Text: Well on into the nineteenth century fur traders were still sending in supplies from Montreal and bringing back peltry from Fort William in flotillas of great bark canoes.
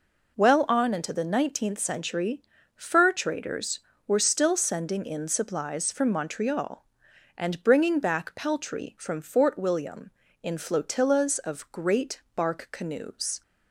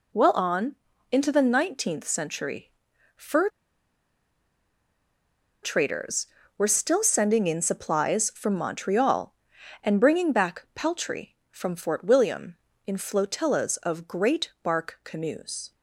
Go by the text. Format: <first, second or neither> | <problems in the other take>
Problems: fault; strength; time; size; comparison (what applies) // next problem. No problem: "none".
first | pauses between "on" and "into"; slight; at 0.7 s; 0.36 s long // pauses between "century" and "fur"; noticeable; at 2.7 s; 0.46 s long; slight in the first // pauses between "fur" and "traders"; strong; at 3.4 s; 2.1 s long